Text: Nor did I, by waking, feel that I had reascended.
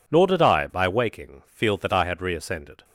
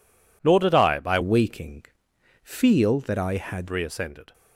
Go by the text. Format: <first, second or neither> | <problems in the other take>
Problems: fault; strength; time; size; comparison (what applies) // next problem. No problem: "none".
first | changes voice from "waking" to "had"; from 1.2 to 3.6 s; 2.4 s long